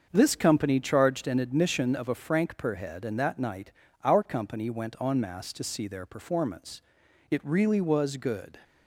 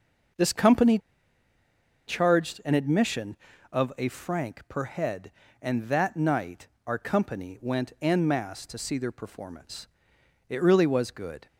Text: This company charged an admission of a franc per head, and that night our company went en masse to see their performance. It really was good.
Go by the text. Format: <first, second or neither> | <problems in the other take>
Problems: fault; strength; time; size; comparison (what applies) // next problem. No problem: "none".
first | starts louder than the rest; until 2.4 s; 6 dB; also in the first // pauses between "company" and "charged"; at 0.9 s; 1.0 s long // pauses between "night" and "our"; slight; at 6.6 s; 0.20 s long; slight in the first